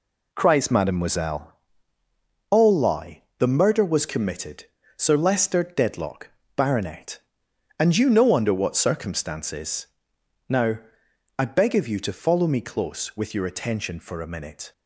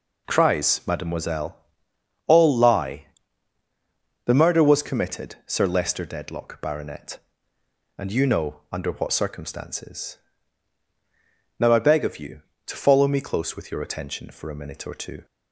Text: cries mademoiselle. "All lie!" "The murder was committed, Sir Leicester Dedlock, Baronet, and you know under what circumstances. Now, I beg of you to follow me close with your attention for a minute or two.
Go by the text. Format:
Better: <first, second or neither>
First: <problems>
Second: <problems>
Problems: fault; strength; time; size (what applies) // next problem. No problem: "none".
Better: second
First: stops before "or two"; at 14.7 s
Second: none